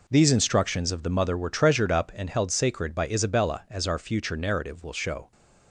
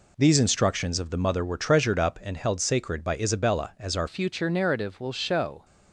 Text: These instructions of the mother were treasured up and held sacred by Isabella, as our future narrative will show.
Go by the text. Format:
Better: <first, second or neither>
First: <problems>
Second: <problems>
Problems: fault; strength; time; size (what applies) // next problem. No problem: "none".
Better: first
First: none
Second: changes voice at "future"; from 4.0 s on; 1.6 s long